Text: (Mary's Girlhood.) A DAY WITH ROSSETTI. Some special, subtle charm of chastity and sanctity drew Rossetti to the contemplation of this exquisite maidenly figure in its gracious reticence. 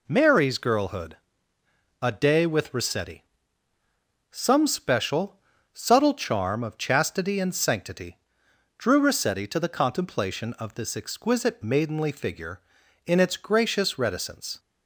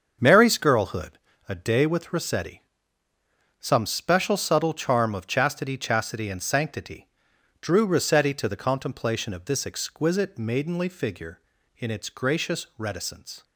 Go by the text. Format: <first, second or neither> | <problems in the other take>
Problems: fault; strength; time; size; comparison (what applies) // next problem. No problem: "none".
first | starts louder than the rest; until 1.5 s; 6.5 dB // says "chastity" twice; at 5.7 s // pauses between "sanctity" and "drew"; noticeable; at 7.0 s; 0.54 s long; noticeable in the first